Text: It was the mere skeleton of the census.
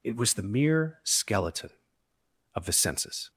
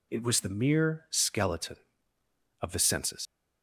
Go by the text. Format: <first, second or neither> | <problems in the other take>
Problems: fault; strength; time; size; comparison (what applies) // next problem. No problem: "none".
first | leaves "census" unfinished; at 3.2 s; 115 ms